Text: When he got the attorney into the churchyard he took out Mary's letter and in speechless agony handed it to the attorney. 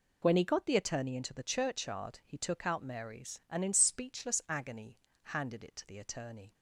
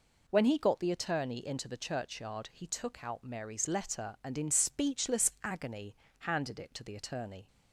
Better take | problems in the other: second | skips "letter"; at 3.4 s // pauses between "agony" and "handed"; slight; at 4.9 s; 0.26 s long; slight in the second

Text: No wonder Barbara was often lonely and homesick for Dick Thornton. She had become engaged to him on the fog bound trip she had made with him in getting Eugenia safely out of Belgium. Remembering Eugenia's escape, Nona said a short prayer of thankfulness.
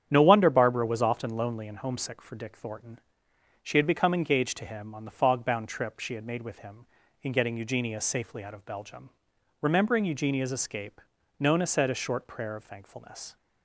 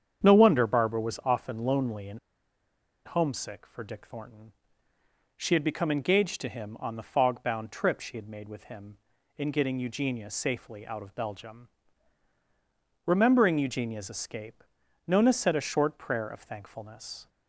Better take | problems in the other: first | starts louder than the rest; strong; until 1.3 s; 8 dB; strong in the first // pauses between "and" and "homesick"; noticeable; at 2.1 s; 0.87 s long

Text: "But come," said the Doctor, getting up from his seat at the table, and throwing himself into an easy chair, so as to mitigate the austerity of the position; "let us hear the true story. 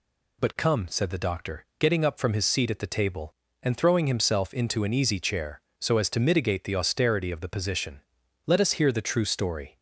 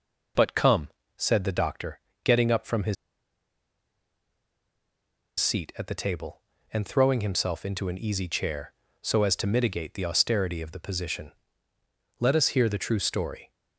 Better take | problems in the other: first | pauses between "his" and "seat"; strong; at 2.9 s; 2.4 s long

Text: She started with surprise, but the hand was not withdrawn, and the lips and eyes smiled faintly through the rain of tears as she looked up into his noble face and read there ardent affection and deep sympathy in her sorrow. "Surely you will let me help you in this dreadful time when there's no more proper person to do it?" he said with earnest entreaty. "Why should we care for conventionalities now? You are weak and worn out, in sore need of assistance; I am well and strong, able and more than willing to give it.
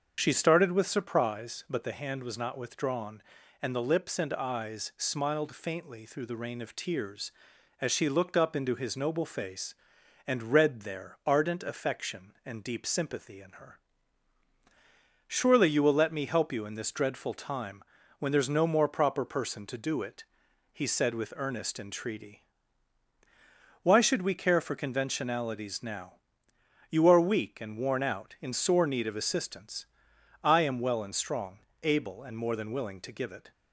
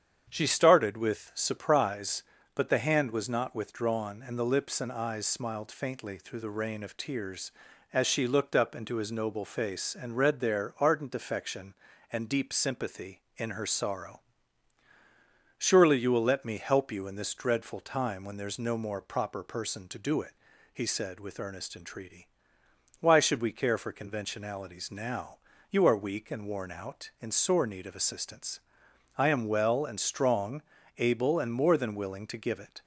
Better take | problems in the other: second | starts louder than the rest; until 1.1 s; 7 dB; strong in the second // skips "sorrow"; at 14.5 s // pauses between "time" and "when"; at 17.8 s; 0.38 s long

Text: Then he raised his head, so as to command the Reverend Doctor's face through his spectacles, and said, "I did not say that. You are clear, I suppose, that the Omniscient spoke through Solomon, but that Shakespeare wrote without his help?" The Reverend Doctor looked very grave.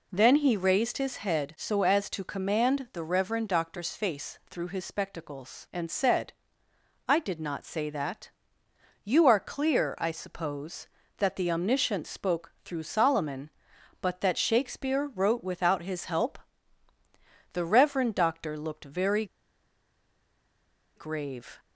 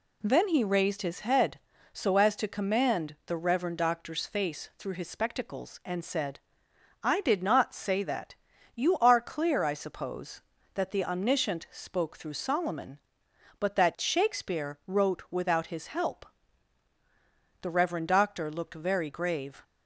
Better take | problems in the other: second | pauses between "very" and "grave"; strong; at 19.2 s; 1.7 s long

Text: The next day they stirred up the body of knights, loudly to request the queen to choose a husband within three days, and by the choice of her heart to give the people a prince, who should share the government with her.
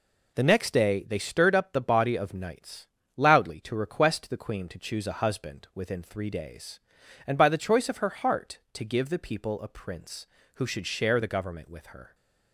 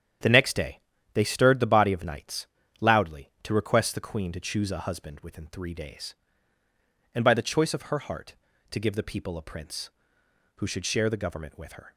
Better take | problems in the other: first | starts louder than the rest; strong; until 1.5 s; 9 dB // pauses between "day" and "they"; at 0.7 s; 0.37 s long // skips "up"; at 1.5 s

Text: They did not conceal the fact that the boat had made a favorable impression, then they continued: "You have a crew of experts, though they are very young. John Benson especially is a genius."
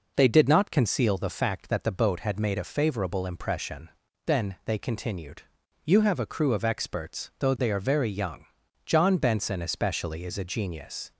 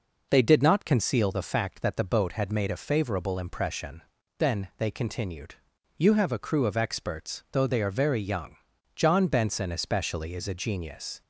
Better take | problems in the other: neither | none

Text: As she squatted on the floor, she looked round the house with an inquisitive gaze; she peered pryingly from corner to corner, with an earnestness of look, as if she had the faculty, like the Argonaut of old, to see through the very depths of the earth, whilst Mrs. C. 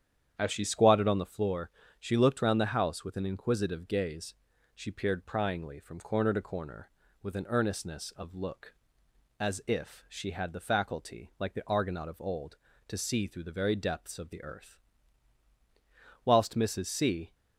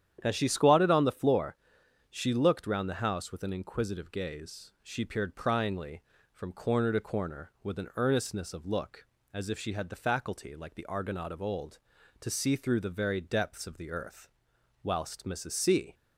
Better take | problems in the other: neither | starts louder than the rest; strong; the same in both

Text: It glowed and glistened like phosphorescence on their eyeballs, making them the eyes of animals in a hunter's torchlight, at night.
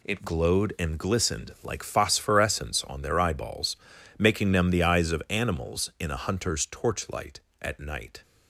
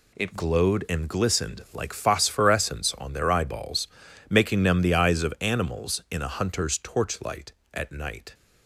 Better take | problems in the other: neither | none

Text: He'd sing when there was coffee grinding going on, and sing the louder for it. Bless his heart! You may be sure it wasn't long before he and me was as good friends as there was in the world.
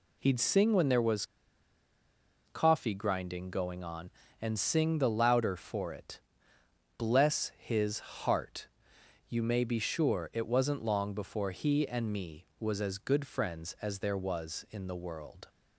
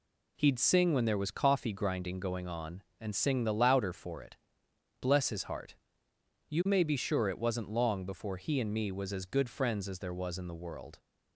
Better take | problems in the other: second | pauses between "was" and "coffee"; at 1.2 s; 1.2 s long

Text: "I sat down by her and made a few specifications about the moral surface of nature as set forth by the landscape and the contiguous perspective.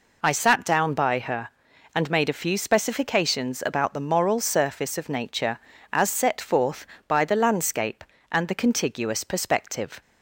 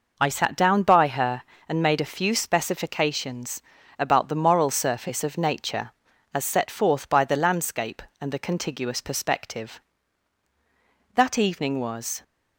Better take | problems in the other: first | pauses between "specifications" and "about"; at 3.6 s; 0.38 s long // goes on to say "That evening was"; noticeable; from 11.1 s on; 1.0 s long

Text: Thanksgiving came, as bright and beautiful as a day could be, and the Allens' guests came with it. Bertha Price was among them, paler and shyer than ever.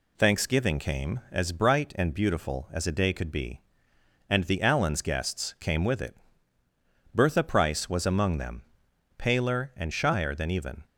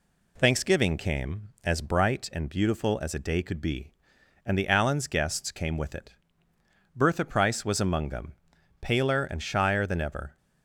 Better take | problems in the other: second | says "even" for "ever"; at 10.5 s

